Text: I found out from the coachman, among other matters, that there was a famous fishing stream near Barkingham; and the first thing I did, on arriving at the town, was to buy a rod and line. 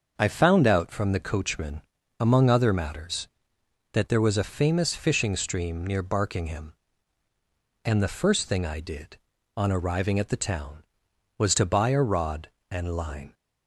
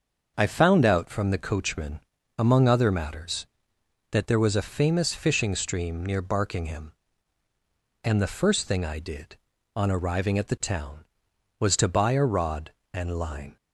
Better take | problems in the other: neither | starts louder than the rest; the same in both

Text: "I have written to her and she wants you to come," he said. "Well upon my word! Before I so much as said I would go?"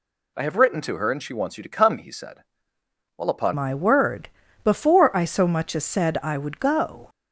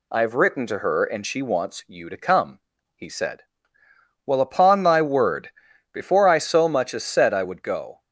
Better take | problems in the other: second | changes voice at "my"; from 3.5 s on; 3.5 s long

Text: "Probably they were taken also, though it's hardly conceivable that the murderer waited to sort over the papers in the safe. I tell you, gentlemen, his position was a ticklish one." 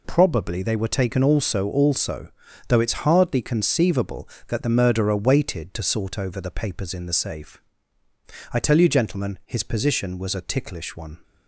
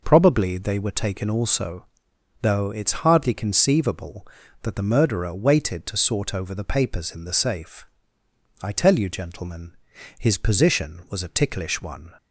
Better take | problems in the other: second | says "also" twice; at 1.6 s

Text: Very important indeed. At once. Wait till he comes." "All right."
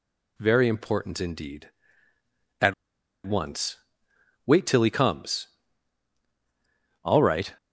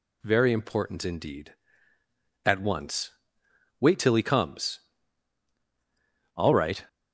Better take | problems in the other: second | pauses between "At" and "once"; noticeable; at 2.7 s; 0.52 s long

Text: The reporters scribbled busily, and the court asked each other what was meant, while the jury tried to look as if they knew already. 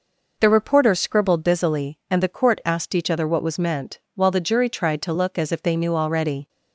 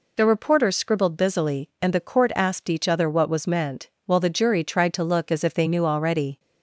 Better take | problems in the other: neither | none

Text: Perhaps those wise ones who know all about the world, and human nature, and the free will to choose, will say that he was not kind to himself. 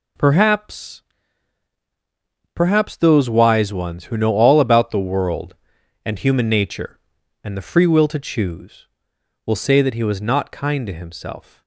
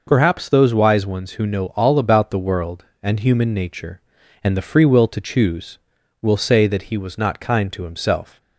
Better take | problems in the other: second | says "Perhaps" twice; at 2.5 s

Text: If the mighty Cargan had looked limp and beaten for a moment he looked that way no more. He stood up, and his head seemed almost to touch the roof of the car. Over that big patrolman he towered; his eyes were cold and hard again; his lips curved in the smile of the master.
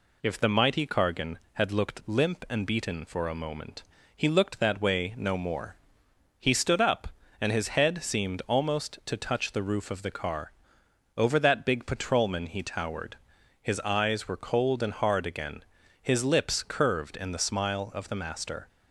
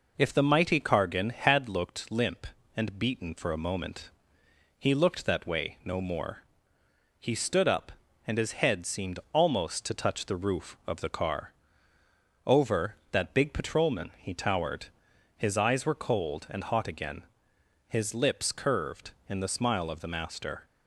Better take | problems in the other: first | pauses between "moment" and "he"; noticeable; at 4.1 s; 0.68 s long; slight in the first // says "hot" for "hard"; at 16.6 s

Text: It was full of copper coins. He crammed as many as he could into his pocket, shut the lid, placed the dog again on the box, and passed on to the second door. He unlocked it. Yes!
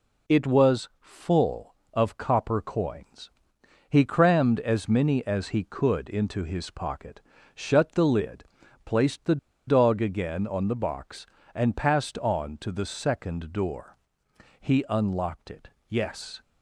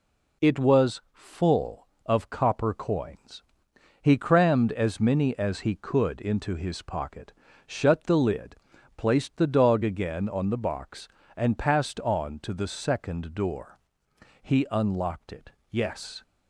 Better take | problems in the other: second | pauses between "the" and "dog"; slight; at 9.3 s; 0.31 s long

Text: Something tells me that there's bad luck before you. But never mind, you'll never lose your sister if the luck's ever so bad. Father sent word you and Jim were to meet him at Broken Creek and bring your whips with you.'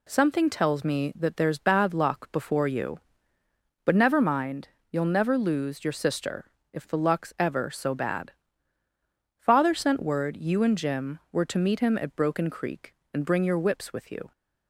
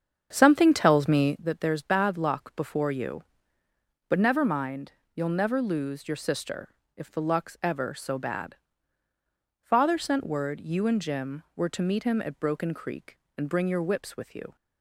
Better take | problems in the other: first | starts louder than the rest; strong; until 1.4 s; 7.5 dB // pauses between "sister" and "if"; slight; at 6.7 s; 0.22 s long; slight in the first

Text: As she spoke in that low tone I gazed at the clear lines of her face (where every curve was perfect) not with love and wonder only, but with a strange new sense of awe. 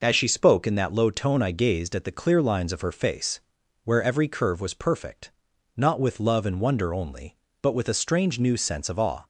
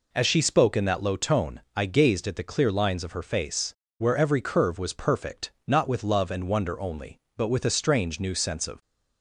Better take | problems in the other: first | pauses between "tone" and "I"; slight; at 1.6 s; 0.16 s long // stops before "awe"; at 8.8 s

